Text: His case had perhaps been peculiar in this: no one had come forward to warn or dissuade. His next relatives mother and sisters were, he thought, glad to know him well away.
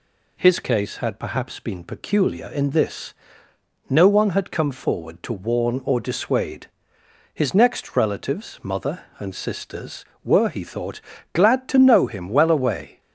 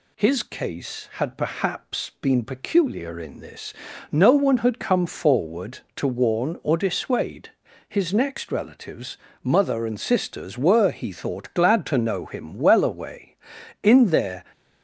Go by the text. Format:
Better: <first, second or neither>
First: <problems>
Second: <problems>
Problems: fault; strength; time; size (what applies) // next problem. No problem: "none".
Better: first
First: none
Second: pauses between "relatives" and "mother"; slight; at 9.1 s; 0.26 s long // goes on to say "In their"; noticeable; from 13.8 s on; 0.62 s long